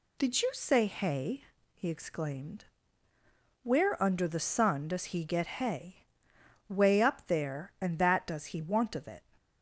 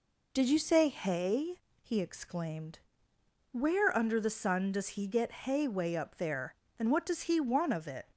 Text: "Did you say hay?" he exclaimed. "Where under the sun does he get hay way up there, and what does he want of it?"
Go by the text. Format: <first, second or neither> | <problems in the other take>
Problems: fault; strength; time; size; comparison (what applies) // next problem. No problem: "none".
second | pauses between "hay" and "way"; noticeable; at 6.0 s; 0.64 s long // says "that" for "what"; at 7.9 s